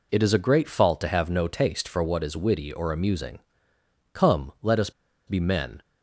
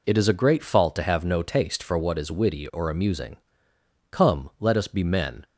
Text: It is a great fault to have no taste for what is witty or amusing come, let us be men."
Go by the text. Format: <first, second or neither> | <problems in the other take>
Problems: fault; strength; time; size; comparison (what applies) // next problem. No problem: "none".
second | pauses between "amusing" and "come"; noticeable; at 3.3 s; 0.74 s long; noticeable in the second // pauses between "us" and "be"; at 4.9 s; 0.36 s long